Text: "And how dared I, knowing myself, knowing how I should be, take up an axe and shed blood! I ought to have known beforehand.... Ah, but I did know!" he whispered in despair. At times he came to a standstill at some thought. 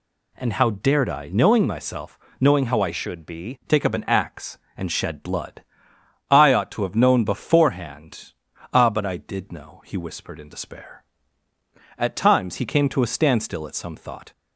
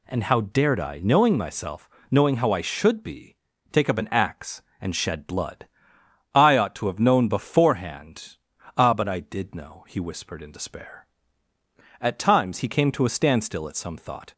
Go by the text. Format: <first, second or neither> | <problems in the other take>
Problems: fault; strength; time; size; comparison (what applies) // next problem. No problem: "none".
second | changes voice from "should" to "be"; from 2.9 to 3.5 s; 0.6 s long